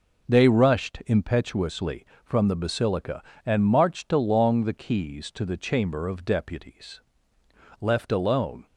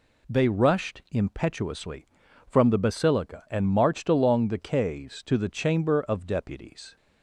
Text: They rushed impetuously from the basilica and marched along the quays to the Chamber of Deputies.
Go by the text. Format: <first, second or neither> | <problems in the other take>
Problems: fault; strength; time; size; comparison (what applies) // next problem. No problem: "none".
second | goes on to say "Left alone"; noticeable; from 7.7 s on; 0.86 s long